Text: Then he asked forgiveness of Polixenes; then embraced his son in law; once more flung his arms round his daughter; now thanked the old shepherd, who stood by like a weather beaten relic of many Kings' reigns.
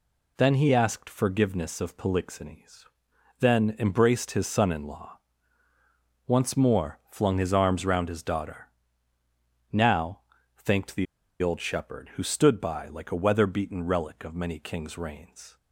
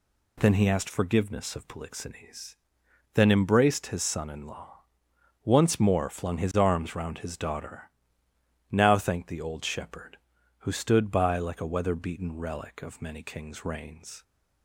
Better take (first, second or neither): second